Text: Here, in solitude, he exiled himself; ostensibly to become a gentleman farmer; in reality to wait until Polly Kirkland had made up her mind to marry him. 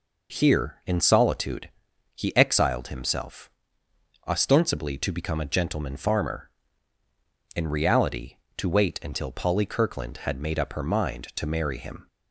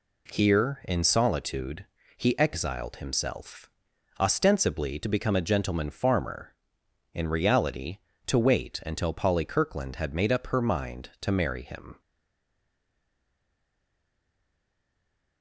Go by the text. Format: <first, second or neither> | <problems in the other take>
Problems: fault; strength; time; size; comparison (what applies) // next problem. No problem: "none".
first | stays silent after the last word; strong; from 12.0 s on; 3.4 s long